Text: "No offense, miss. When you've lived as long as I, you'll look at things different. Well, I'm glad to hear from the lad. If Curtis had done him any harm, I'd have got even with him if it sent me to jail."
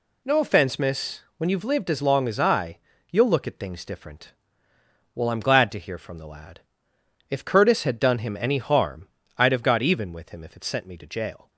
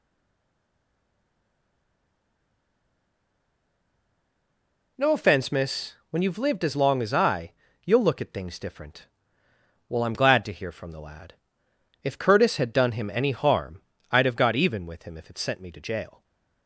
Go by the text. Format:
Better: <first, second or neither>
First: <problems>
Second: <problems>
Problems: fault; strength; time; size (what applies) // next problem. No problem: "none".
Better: first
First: none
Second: stays silent before the first word; strong; until 4.9 s; 4.9 s long // stays silent after the last word; slight; from 16.1 s on; 0.5 s long